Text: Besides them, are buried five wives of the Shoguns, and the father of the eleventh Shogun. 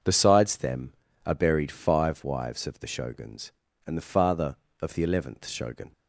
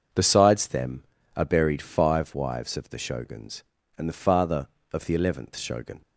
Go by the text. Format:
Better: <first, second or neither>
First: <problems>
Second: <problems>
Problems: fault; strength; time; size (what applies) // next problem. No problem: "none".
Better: neither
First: none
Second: none